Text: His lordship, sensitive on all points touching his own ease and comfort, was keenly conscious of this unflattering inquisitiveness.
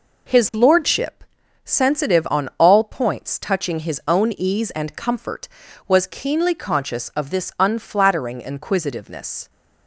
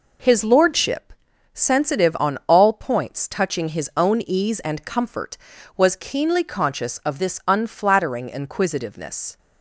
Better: neither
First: none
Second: none

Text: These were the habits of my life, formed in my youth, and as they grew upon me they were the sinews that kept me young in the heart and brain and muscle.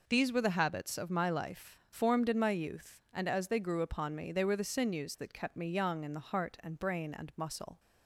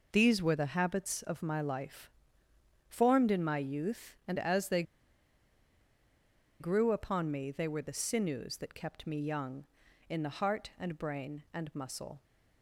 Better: first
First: none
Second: pauses between "they" and "grew"; strong; at 4.8 s; 1.7 s long

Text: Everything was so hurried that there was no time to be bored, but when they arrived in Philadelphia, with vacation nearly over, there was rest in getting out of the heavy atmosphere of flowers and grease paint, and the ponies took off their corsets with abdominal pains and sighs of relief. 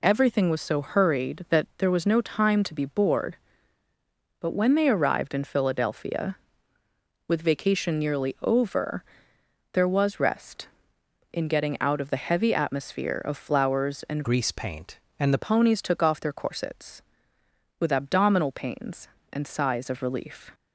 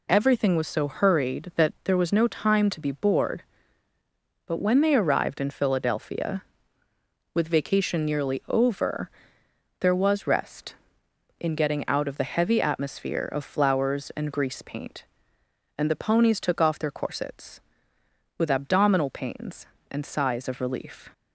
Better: second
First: changes voice from "grease" to "the"; from 14.2 to 15.4 s; 1.2 s long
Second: none

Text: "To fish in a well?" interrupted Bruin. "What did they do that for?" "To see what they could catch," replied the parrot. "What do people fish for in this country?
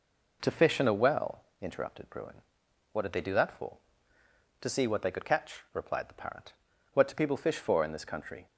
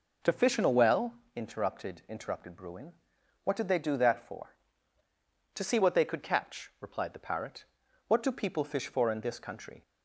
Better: first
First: none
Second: says "interrupted" twice; at 2.0 s

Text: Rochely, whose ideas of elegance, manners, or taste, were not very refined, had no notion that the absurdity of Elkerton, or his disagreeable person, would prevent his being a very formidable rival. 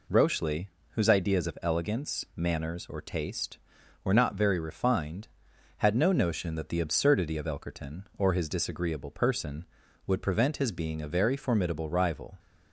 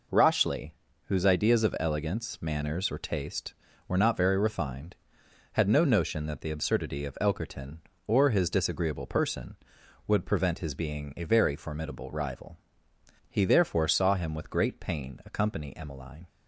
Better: first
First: none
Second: goes on to say "He therefore saw him with great pain accompany Emmeline"; strong; from 13.2 s on; 2.9 s long

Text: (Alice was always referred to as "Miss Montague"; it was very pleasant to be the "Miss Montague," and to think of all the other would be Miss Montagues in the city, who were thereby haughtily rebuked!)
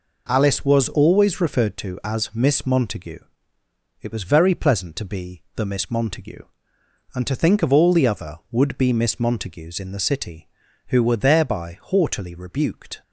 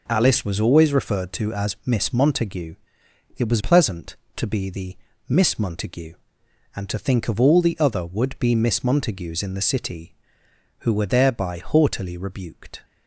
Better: first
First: none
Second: skips "very"; at 3.5 s // pauses between "the" and "Miss"; slight; at 4.9 s; 0.32 s long

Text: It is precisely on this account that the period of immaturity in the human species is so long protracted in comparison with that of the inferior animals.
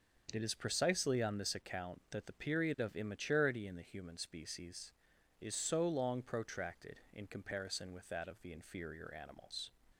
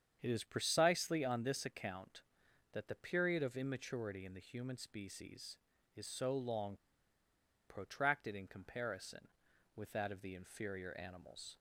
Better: first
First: starts louder than the rest; until 1.3 s; 6.5 dB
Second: starts louder than the rest; strong; until 1.2 s; 8 dB // pauses between "long" and "protracted"; noticeable; at 6.7 s; 0.90 s long

